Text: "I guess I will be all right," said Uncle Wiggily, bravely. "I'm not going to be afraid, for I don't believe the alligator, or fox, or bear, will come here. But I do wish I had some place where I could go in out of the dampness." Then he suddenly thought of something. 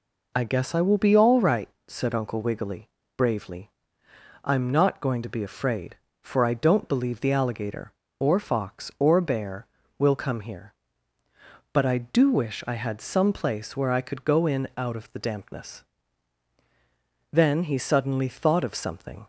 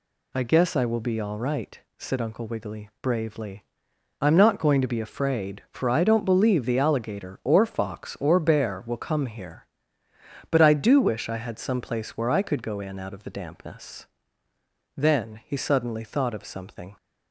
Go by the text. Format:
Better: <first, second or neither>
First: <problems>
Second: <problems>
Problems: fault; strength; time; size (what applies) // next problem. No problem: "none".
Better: neither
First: none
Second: none